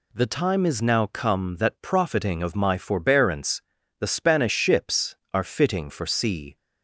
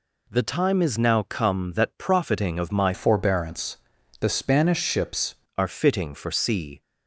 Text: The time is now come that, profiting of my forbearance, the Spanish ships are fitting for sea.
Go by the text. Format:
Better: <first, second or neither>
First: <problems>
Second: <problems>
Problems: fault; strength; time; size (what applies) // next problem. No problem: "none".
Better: first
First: none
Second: changes voice from "forbearance" to "ships"; from 2.9 to 5.3 s; 2.4 s long